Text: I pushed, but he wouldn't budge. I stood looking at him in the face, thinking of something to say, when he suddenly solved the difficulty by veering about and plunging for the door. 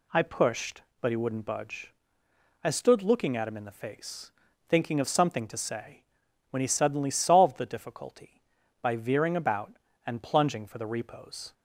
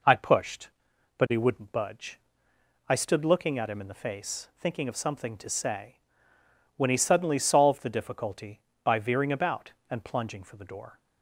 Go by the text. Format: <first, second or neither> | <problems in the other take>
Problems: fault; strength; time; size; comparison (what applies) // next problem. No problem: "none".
second | says "repos" for "door"; at 10.8 s